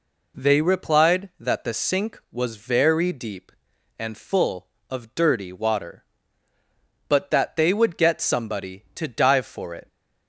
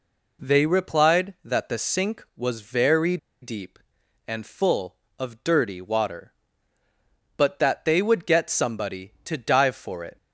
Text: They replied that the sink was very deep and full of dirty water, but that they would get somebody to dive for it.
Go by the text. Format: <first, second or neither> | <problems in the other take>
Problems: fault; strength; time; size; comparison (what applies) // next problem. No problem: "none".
first | pauses between "very" and "deep"; slight; at 3.1 s; 0.23 s long